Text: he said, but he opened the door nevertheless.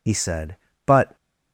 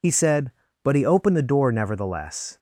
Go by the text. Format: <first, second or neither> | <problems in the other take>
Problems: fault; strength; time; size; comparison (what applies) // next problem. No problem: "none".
second | stops before "he opened the door nevertheless"; at 1.1 s